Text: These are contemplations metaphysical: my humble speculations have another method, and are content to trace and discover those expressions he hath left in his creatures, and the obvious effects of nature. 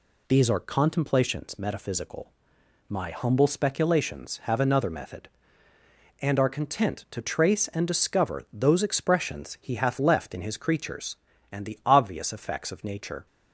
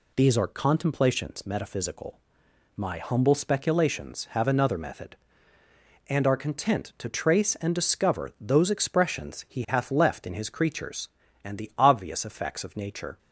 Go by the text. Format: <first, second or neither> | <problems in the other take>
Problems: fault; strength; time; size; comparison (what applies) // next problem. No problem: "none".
neither | none